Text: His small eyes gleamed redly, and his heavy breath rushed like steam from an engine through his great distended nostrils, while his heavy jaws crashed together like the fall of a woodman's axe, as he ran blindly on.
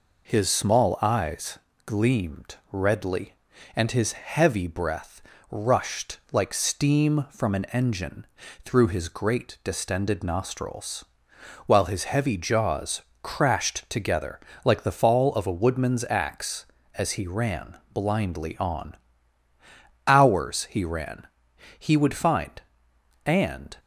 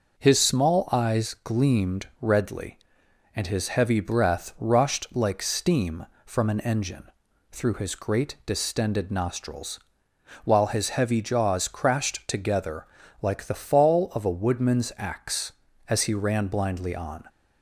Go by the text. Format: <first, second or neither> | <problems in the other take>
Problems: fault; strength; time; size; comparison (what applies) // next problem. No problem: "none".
second | pauses between "eyes" and "gleamed"; slight; at 1.5 s; 0.26 s long // pauses between "gleamed" and "redly"; slight; at 2.5 s; 0.16 s long // pauses between "breath" and "rushed"; slight; at 5.2 s; 0.30 s long // pauses between "engine" and "through"; at 8.2 s; 0.38 s long; also in the second // pauses between "jaws" and "crashed"; slight; at 13.0 s; 0.18 s long // pauses between "together" and "like"; slight; at 14.3 s; 0.24 s long; slight in the second // pauses between "ran" and "blindly"; slight; at 17.7 s; 0.16 s long // goes on to say "Hours he ran he would find and"; strong; from 20.0 s on; 3.7 s long